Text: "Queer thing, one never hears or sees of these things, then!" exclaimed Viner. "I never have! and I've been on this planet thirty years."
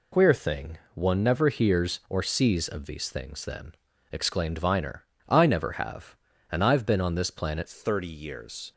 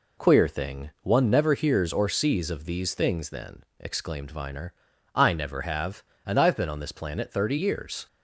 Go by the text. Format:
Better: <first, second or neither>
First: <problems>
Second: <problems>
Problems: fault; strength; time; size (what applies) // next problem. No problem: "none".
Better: second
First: changes voice at "thirty"; from 7.6 s on; 1.1 s long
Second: none